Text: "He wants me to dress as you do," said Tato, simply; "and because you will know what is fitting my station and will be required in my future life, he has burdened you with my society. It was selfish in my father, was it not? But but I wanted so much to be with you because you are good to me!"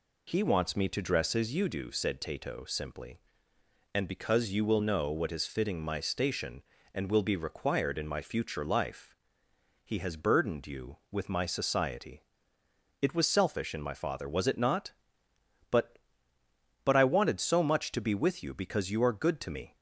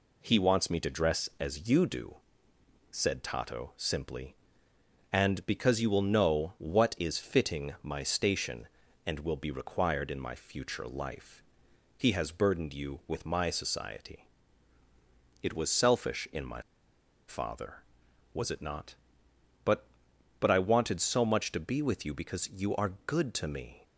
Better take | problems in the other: first | pauses between "my" and "father"; noticeable; at 16.6 s; 0.65 s long

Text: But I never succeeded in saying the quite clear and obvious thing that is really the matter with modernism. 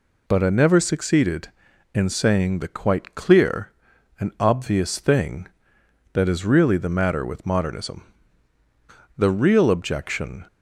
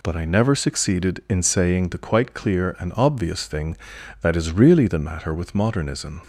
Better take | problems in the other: second | goes on to say "The real objection"; noticeable; from 9.1 s on; 1.3 s long

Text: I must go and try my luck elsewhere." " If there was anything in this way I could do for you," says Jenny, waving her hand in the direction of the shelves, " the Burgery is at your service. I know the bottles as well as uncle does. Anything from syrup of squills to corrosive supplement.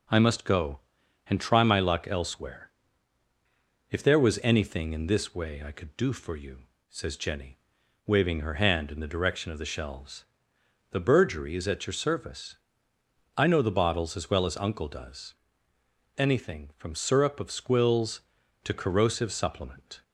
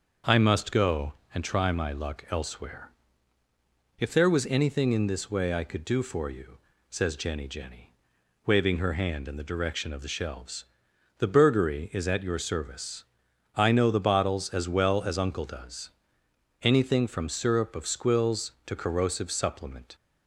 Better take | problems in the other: first | says "Jenny" twice; at 7.4 s

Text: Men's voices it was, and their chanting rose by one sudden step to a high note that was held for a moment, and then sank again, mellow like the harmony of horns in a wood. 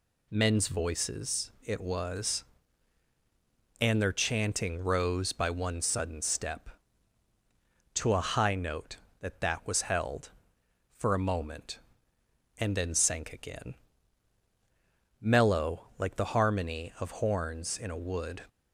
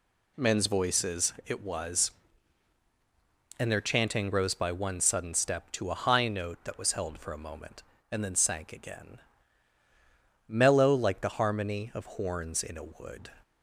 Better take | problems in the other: second | says "that" twice; at 9.3 s

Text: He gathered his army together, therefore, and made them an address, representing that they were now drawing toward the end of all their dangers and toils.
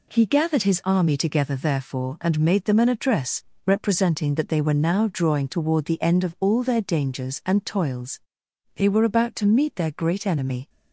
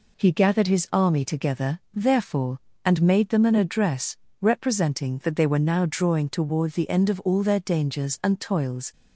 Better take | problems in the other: second | goes on to say "They were about to meet their great enemy"; strong; from 8.7 s on; 1.9 s long

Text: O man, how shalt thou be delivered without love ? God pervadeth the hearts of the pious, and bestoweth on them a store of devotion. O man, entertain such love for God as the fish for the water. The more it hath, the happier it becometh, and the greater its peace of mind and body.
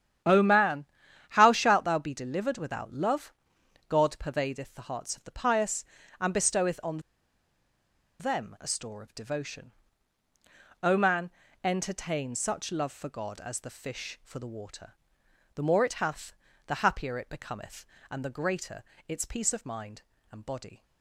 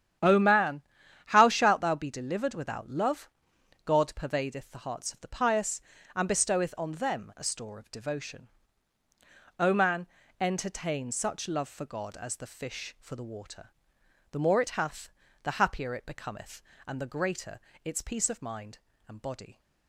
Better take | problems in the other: second | starts louder than the rest; strong; until 1.7 s; 10 dB; strong in the second // pauses between "on" and "them"; at 6.9 s; 1.2 s long // pauses between "greater" and "its"; slight; at 18.8 s; 0.24 s long; slight in the second

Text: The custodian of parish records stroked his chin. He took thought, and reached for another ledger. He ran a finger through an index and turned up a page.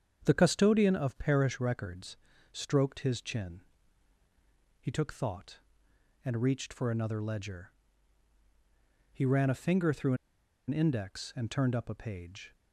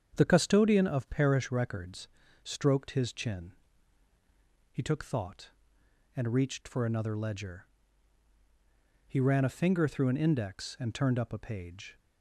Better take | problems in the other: second | starts louder than the rest; strong; until 1.2 s; 7.5 dB; strong in the second // pauses between "records" and "stroked"; slight; at 2.1 s; 0.36 s long; slight in the second // pauses between "through" and "an"; noticeable; at 10.1 s; 0.53 s long

